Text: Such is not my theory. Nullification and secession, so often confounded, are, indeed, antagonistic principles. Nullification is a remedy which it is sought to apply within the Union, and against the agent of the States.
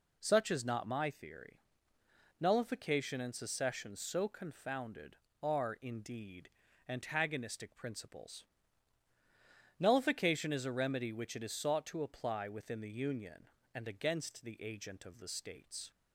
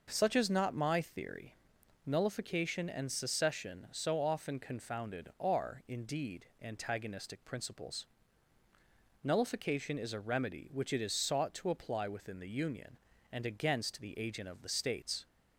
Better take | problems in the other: second | skips "often"; at 4.2 s

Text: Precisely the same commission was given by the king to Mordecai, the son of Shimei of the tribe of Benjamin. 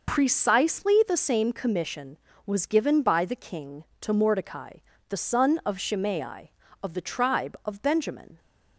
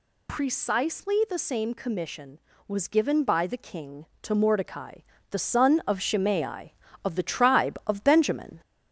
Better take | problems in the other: first | gets louder; slight; throughout; 2 dB

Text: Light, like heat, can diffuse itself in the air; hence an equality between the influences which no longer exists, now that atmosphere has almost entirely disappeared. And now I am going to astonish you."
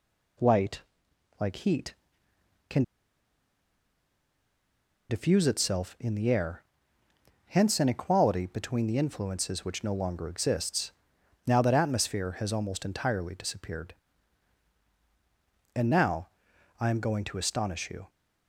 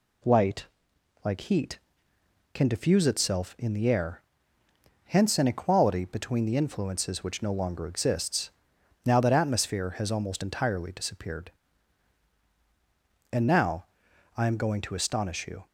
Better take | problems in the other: second | pauses between "can" and "diffuse"; strong; at 2.8 s; 2.2 s long // pauses between "now" and "I"; noticeable; at 16.2 s; 0.52 s long; noticeable in the second

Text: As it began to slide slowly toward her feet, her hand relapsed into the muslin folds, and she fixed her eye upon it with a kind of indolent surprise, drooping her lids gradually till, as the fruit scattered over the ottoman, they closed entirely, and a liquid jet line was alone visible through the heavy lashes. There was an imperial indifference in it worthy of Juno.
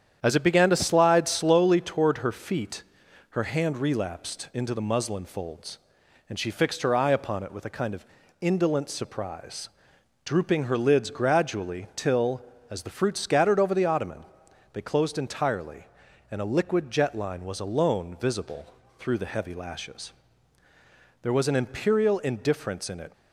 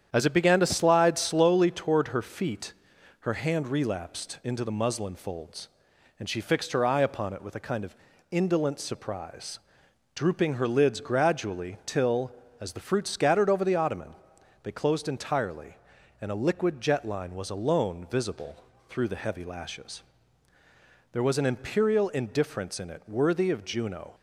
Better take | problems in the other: second | starts louder than the rest; strong; until 1.2 s; 9 dB; strong in the second // pauses between "of" and "indolent"; slight; at 8.0 s; 0.36 s long; slight in the second // pauses between "visible" and "through"; slight; at 18.6 s; 0.32 s long; slight in the second // stops before "worthy of Juno"; at 23.1 s

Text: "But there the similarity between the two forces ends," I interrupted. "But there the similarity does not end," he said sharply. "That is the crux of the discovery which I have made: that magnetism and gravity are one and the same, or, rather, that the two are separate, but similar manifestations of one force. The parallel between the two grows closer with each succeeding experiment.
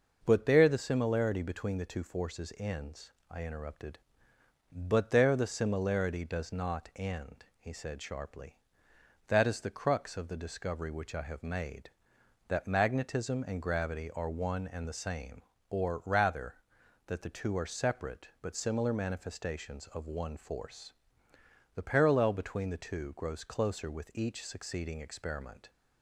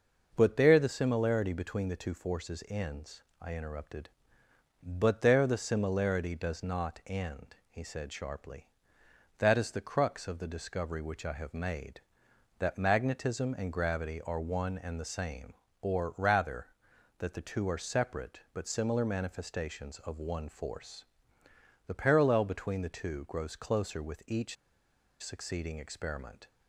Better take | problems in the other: first | pauses between "each" and "succeeding"; noticeable; at 24.5 s; 0.66 s long

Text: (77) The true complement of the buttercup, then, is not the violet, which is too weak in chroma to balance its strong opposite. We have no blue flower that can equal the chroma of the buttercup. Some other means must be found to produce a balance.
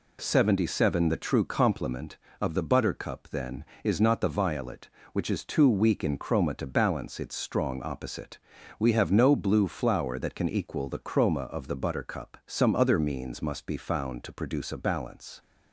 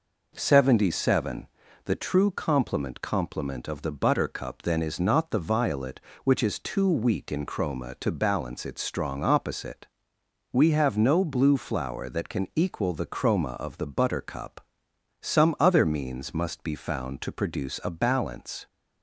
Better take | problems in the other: first | says "complement" twice; at 3.0 s

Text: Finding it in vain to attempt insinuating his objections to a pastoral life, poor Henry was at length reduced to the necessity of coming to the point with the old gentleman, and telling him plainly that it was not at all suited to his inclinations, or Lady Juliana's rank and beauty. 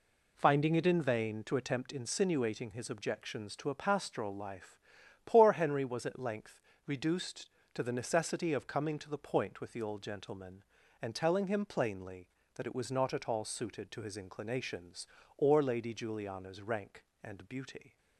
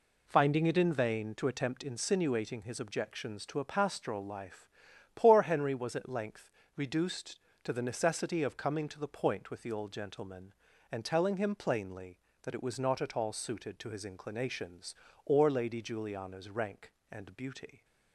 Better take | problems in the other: neither | pauses between "length" and "reduced"; slight; the same in both

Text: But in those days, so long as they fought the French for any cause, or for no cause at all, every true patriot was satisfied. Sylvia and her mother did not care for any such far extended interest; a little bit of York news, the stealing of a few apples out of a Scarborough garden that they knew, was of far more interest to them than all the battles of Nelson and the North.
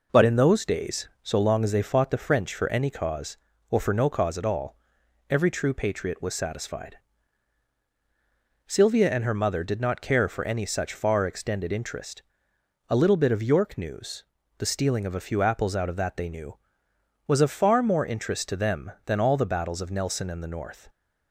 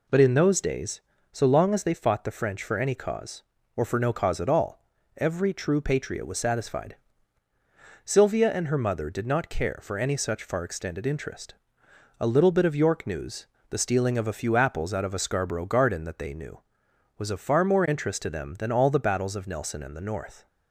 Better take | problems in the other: second | skips "a Scarborough garden"; at 15.9 s

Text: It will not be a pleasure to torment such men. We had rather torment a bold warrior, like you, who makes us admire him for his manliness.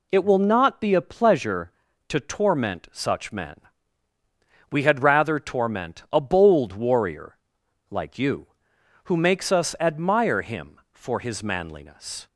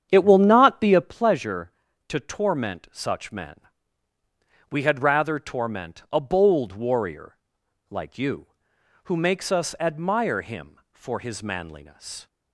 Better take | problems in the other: first | starts louder than the rest; strong; until 1.2 s; 8.5 dB

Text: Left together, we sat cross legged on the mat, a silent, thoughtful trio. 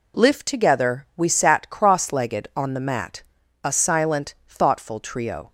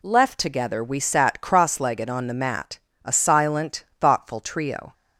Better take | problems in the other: second | says "Lift" for "Left"; at 0.1 s

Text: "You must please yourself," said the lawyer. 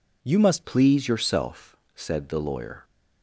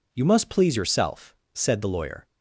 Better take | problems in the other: second | changes voice at "please"; from 0.6 s on; 2.2 s long

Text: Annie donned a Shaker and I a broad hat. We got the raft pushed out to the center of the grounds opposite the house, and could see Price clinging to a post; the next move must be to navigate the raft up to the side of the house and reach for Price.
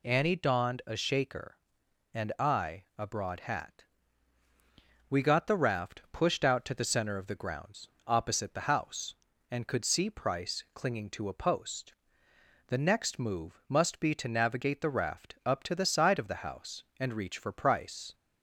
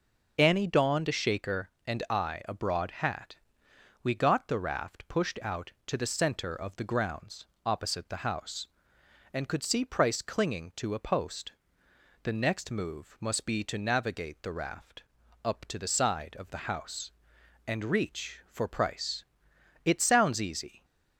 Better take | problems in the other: first | pauses between "grounds" and "opposite"; slight; at 7.4 s; 0.18 s long; slight in the first // pauses between "raft" and "up"; at 15.0 s; 0.40 s long // goes on to say "It sounds easy"; noticeable; from 19.8 s on; 1.0 s long

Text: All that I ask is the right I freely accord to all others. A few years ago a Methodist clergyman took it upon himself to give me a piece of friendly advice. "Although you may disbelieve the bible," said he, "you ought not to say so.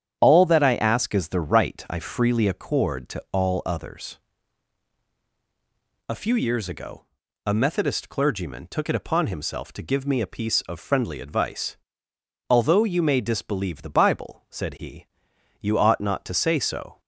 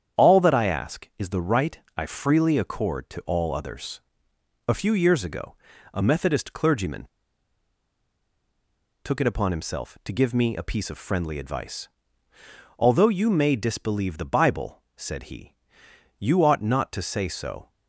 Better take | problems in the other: first | starts louder than the rest; strong; until 1.2 s; 8.5 dB; strong in the first // pauses between "right" and "I"; slight; at 1.7 s; 0.16 s long // pauses between "ago" and "a"; at 5.5 s; 0.40 s long; also in the first // pauses between "clergyman" and "took"; strong; at 7.0 s; 1.9 s long

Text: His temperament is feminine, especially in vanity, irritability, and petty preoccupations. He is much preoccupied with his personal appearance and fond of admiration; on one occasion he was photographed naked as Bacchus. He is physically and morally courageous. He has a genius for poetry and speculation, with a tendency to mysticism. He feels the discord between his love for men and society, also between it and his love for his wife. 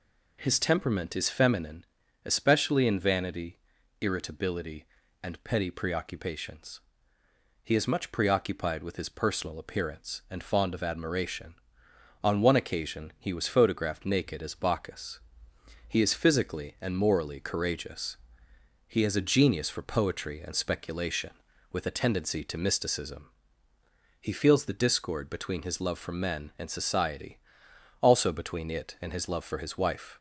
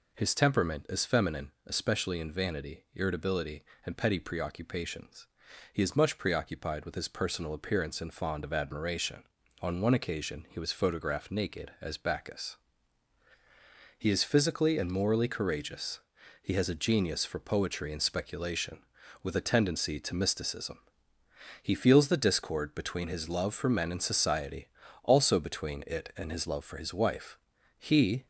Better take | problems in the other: first | goes on to say "He"; slight; from 27.8 s on; 0.46 s long

